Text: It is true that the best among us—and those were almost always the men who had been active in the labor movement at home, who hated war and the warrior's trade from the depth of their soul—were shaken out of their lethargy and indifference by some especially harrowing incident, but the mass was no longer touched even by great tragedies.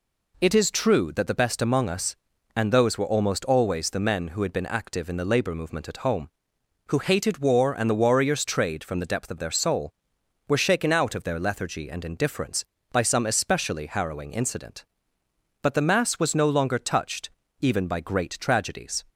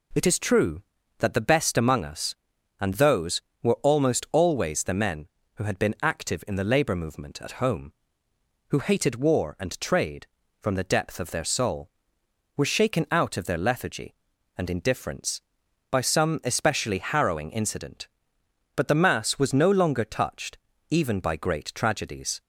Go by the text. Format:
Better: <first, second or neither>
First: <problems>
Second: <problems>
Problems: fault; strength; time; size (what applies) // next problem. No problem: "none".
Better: first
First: pauses between "touched" and "even"; slight; at 17.2 s; 0.32 s long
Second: skips "the warrior's"; at 9.7 s // pauses between "touched" and "even"; slight; at 20.5 s; 0.32 s long